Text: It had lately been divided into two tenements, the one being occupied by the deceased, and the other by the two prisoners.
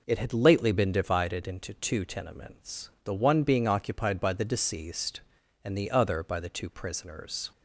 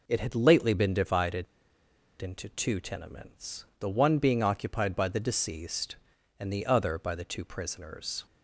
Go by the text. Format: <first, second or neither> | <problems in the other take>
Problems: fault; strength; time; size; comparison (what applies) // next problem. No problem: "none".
first | pauses between "divided" and "into"; noticeable; at 1.4 s; 0.75 s long